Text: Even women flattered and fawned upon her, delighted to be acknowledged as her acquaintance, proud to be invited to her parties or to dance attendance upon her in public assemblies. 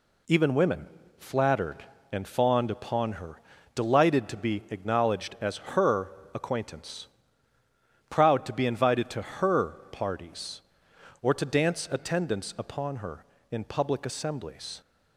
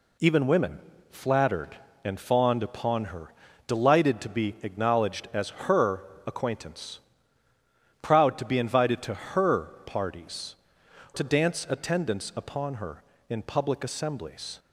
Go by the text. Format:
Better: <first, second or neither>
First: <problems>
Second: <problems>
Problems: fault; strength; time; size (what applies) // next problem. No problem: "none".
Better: first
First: pauses between "women" and "flattered"; slight; at 0.8 s; 0.32 s long // pauses between "her" and "acquaintance"; slight; at 6.1 s; 0.24 s long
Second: pauses between "women" and "flattered"; slight; at 0.7 s; 0.32 s long // pauses between "her" and "acquaintance"; slight; at 6.0 s; 0.24 s long // skips "or"; at 10.8 s